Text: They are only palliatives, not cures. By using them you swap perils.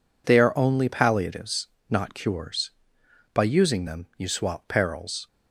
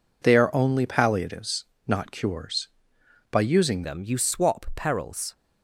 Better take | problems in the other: first | changes voice at "them"; from 3.8 s on; 1.5 s long

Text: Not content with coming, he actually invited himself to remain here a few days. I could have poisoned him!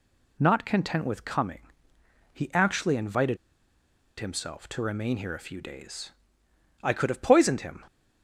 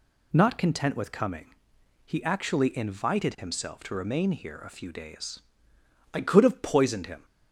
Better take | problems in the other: second | pauses between "invited" and "himself"; noticeable; at 3.3 s; 0.82 s long

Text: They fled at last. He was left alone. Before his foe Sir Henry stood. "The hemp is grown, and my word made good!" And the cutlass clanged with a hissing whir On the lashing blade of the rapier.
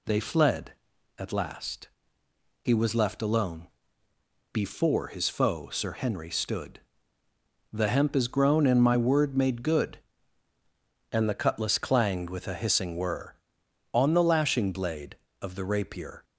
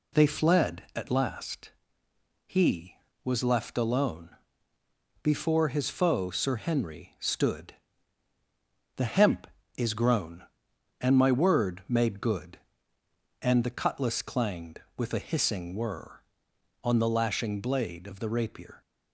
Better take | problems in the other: neither | none

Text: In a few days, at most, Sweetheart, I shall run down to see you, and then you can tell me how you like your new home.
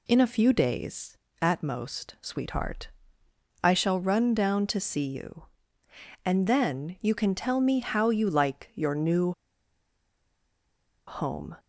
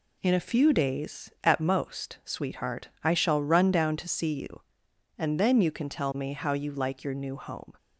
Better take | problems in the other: second | pauses between "new" and "home"; strong; at 9.3 s; 1.7 s long

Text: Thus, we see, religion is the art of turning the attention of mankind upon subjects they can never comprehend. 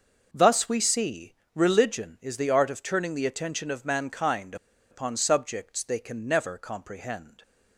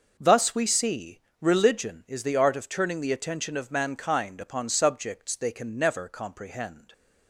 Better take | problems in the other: second | pauses between "mankind" and "upon"; slight; at 4.5 s; 0.35 s long

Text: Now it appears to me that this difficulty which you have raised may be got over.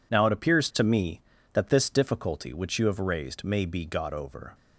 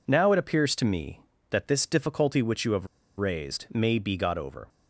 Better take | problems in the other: first | pauses between "have" and "raised"; slight; at 2.8 s; 0.30 s long

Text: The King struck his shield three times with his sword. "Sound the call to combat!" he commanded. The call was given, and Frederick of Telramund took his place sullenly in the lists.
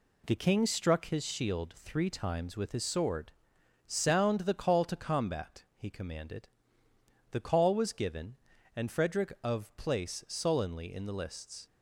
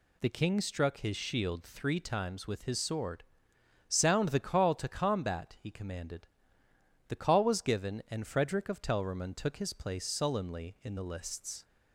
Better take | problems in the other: second | skips "Telramund took his"; at 9.7 s

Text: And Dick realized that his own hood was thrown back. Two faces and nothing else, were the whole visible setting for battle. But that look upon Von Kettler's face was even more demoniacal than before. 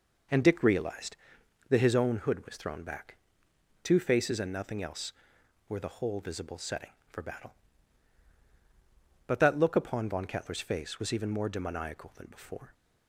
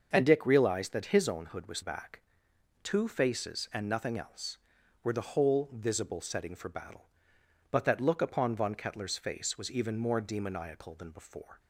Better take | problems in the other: first | starts louder than the rest; until 1.1 s; 6 dB // skips "thrown"; at 1.8 s

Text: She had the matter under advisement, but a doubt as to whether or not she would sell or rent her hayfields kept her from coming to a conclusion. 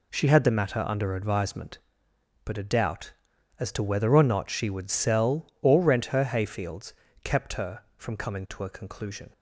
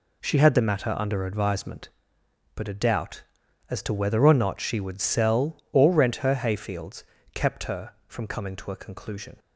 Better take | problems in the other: neither | pauses between "hayfields" and "kept"; slight; the same in both

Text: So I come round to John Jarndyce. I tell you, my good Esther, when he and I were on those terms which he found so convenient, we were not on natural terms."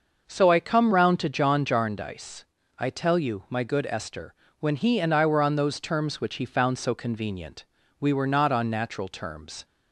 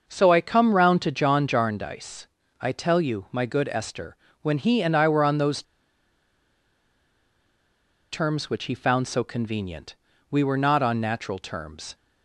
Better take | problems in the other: first | starts louder than the rest; until 1.0 s; 6 dB; also in the first // pauses between "those" and "terms"; strong; at 5.6 s; 2.4 s long

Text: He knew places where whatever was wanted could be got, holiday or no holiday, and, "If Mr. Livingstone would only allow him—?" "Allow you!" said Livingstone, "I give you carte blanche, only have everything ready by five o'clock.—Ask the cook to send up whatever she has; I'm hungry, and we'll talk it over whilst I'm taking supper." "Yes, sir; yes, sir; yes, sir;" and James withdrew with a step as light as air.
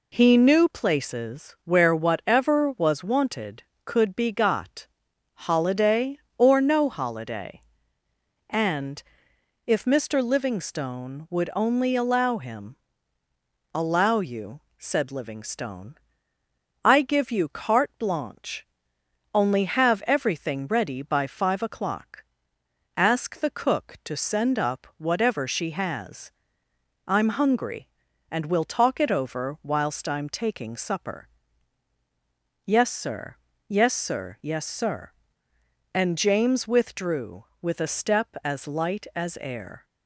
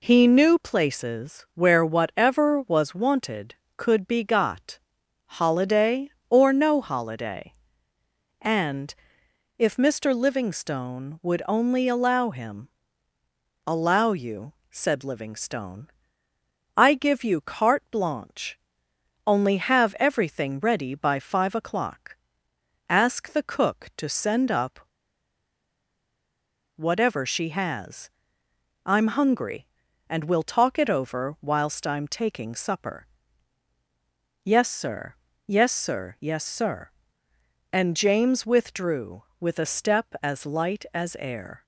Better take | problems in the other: first | pauses between "up" and "whatever"; strong; at 24.8 s; 1.9 s long

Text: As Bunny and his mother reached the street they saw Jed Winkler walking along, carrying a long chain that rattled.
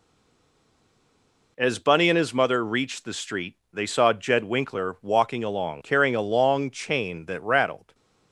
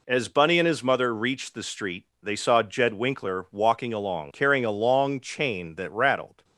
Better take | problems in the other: second | stays silent before the first word; noticeable; until 1.5 s; 1.5 s long // pauses between "street" and "they"; slight; at 3.5 s; 0.18 s long; slight in the second

